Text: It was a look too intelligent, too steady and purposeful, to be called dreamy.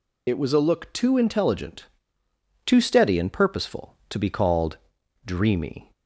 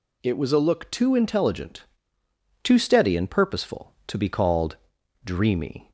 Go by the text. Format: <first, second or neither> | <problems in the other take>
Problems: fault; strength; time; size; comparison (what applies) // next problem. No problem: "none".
second | loses the start of "It"; at 0.2 s; 40 ms // pauses between "called" and "dreamy"; noticeable; at 4.7 s; 0.46 s long; noticeable in the second